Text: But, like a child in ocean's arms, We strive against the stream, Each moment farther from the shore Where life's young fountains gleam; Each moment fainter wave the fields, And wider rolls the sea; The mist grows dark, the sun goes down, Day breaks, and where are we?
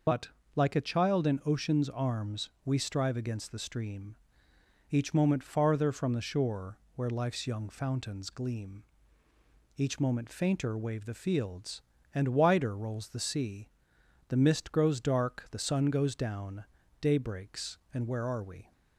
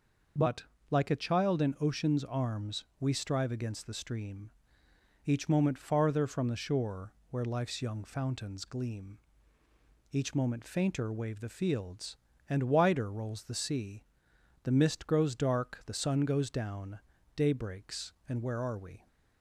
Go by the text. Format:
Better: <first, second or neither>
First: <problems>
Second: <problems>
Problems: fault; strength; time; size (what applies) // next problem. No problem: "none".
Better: second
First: loses the start of "But"; at 0.0 s; 60 ms // pauses between "shore" and "Where"; slight; at 6.7 s; 0.20 s long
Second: pauses between "shore" and "Where"; slight; at 7.1 s; 0.20 s long